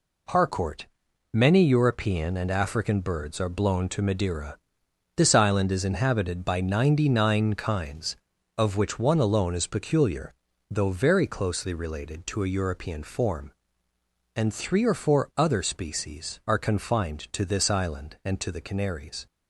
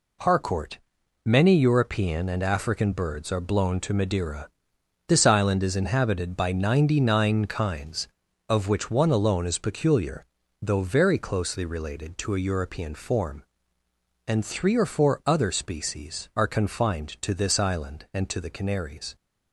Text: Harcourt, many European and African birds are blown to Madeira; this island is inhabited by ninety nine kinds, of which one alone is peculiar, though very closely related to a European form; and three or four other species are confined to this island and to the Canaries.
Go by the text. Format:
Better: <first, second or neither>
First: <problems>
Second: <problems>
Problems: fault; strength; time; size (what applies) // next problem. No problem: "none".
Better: neither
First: none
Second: none